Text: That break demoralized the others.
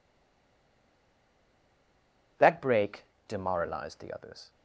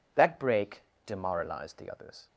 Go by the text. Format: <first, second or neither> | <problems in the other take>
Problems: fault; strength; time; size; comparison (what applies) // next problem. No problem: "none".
second | stays silent before the first word; until 2.3 s; 2.3 s long // pauses between "break" and "demoralized"; slight; at 3.0 s; 0.24 s long; slight in the second